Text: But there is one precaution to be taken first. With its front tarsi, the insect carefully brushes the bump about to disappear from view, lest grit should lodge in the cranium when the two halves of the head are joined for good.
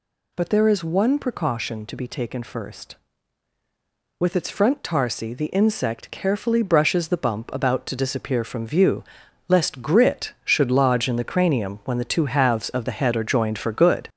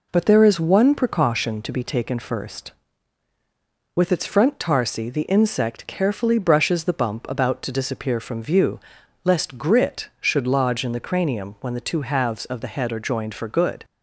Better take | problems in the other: second | gets louder; noticeable; throughout; 5.5 dB

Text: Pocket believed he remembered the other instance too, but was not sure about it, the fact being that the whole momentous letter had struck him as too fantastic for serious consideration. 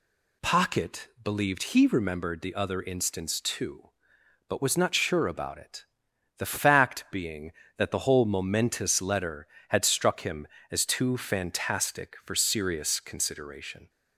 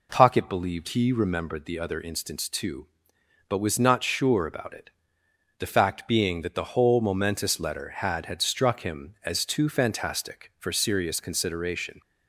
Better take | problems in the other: first | says "had" twice; at 8.2 s

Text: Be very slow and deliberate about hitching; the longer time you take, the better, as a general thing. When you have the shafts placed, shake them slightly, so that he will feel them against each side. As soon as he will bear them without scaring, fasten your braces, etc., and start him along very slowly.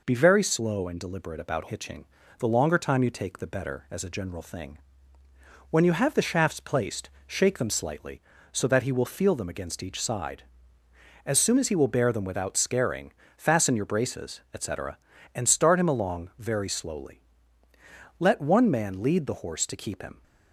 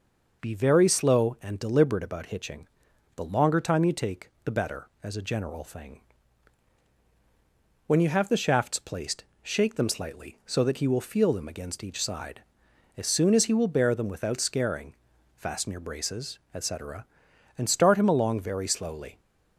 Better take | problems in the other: second | goes on to say "Let one man lead the horse to keep him"; strong; from 18.1 s on; 2.0 s long

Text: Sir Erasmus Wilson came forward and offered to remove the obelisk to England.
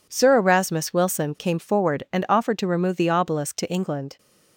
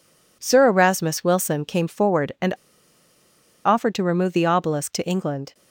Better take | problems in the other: first | pauses between "and" and "offered"; at 2.5 s; 1.1 s long

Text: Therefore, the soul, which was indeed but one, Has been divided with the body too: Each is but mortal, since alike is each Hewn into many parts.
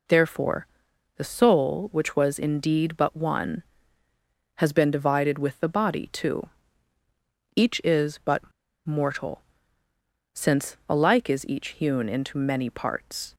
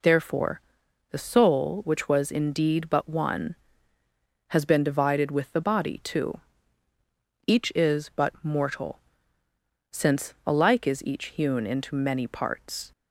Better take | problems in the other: second | pauses between "but" and "mortal"; at 8.4 s; 0.43 s long

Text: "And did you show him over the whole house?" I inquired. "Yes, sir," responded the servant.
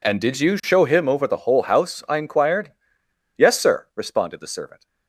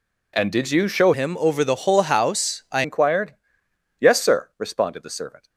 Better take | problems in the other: first | changes voice from "him" to "I"; from 1.1 to 2.8 s; 1.7 s long

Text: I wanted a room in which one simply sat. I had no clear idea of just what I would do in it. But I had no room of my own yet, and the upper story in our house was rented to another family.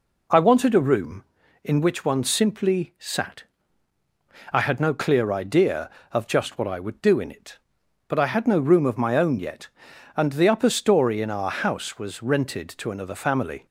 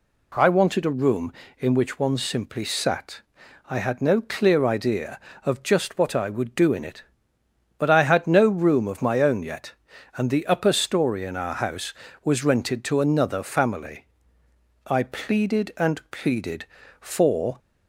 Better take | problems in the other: first | goes on to say "I pleaded and pleaded for"; strong; from 14.8 s on; 2.7 s long

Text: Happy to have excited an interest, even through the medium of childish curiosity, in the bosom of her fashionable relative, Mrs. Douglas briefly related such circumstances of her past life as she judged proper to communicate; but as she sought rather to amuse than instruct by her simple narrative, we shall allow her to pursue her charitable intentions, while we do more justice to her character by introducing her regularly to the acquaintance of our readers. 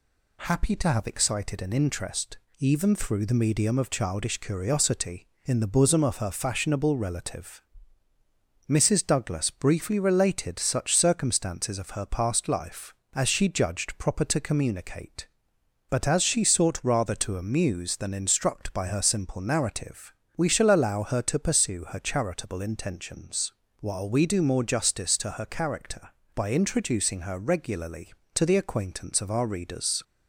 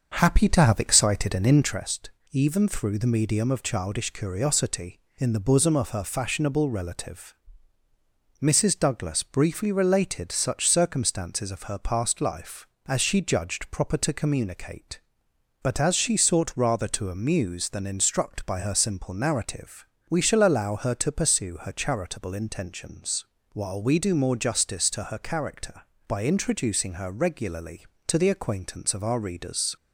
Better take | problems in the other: first | starts louder than the rest; until 1.9 s; 6.5 dB

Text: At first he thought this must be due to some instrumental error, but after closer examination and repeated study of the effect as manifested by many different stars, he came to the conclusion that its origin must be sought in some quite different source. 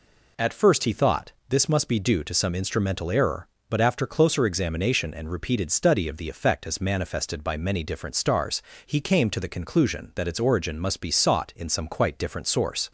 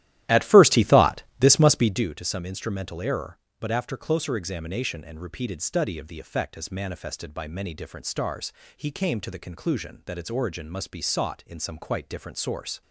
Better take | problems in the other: first | starts louder than the rest; strong; until 2.1 s; 13.5 dB // pauses between "thought" and "this"; slight; at 1.2 s; 0.18 s long; slight in the first

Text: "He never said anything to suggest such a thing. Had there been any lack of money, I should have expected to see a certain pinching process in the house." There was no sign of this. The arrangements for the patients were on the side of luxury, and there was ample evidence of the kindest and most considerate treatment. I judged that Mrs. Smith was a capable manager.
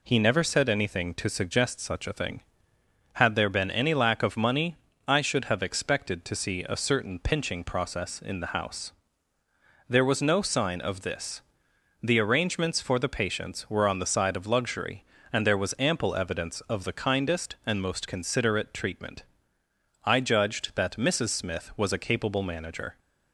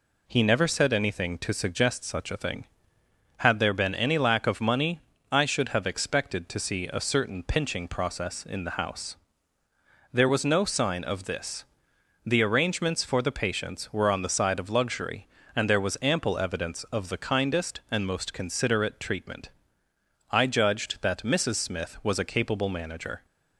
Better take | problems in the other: neither | none

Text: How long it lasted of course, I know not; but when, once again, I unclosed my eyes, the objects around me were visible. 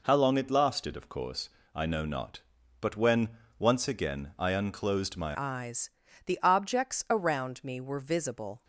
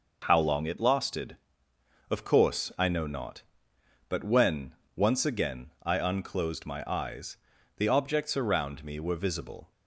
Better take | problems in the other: second | changes voice at "eyes"; from 5.3 s on; 3.3 s long

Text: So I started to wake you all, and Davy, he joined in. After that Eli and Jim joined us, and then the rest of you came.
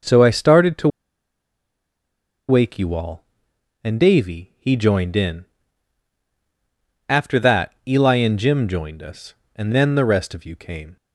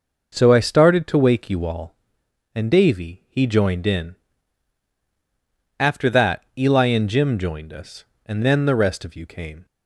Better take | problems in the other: second | pauses between "to" and "wake"; strong; at 0.8 s; 1.6 s long // pauses between "that" and "Eli"; slight; at 7.7 s; 0.16 s long; slight in the second

